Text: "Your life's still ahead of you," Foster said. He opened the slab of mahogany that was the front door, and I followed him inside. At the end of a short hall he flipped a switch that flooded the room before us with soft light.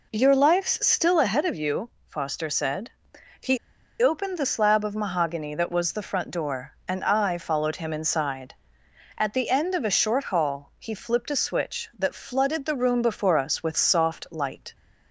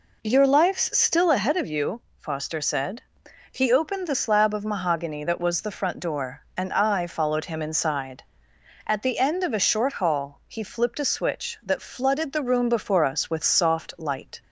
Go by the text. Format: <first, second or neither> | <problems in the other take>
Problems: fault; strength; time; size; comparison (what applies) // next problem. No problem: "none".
second | pauses between "He" and "opened"; at 3.5 s; 0.44 s long